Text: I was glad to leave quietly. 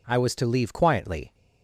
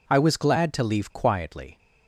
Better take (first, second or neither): second